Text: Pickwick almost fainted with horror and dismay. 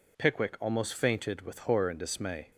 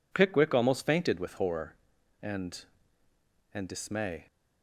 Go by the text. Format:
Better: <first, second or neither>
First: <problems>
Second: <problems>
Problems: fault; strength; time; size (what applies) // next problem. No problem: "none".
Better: first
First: none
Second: says "and" twice; at 3.5 s